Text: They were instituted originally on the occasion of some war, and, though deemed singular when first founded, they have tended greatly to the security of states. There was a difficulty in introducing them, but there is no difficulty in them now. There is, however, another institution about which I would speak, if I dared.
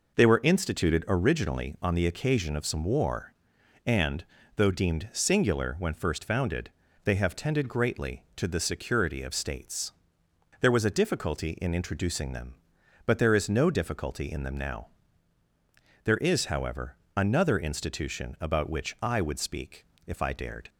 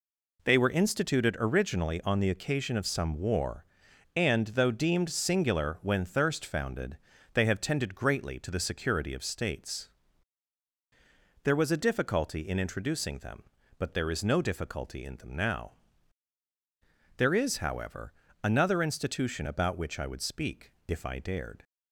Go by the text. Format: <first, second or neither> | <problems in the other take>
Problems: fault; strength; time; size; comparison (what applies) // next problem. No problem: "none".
first | says "thirst" for "first"; at 6.0 s